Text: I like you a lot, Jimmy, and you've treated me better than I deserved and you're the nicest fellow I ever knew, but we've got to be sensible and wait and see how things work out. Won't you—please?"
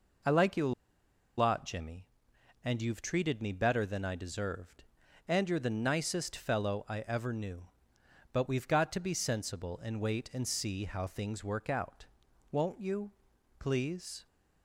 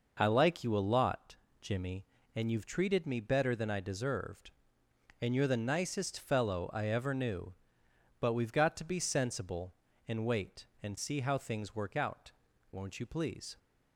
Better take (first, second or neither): second